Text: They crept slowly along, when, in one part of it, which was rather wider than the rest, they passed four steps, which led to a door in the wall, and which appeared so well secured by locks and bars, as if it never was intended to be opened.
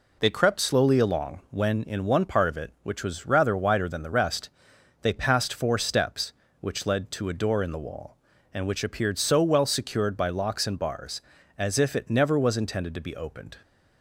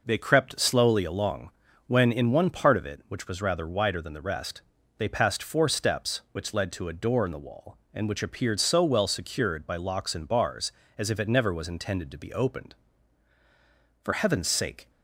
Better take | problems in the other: first | goes on to say "For heaven's sake"; noticeable; from 14.0 s on; 0.86 s long

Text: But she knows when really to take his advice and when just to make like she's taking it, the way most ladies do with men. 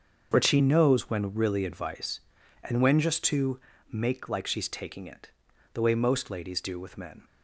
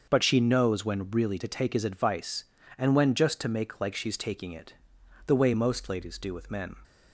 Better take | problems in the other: second | starts louder than the rest; until 1.3 s; 7 dB; also in the second // skips "to take his"; at 1.6 s // pauses between "to" and "make"; slight; at 3.5 s; 0.32 s long

